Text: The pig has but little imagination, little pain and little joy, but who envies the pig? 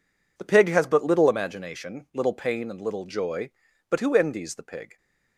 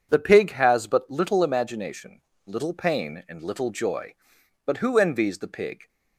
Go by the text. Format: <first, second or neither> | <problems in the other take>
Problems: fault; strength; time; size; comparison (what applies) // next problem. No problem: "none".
second | gets quieter; strong; throughout; 11 dB